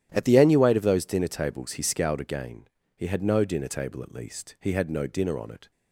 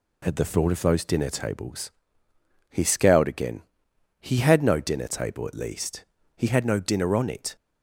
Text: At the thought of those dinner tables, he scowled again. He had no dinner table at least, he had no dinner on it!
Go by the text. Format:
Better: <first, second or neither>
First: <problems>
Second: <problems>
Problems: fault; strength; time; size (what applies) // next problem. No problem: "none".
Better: second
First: starts louder than the rest; strong; until 1.1 s; 11.5 dB // says "annuate" for "thought"; at 0.3 s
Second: none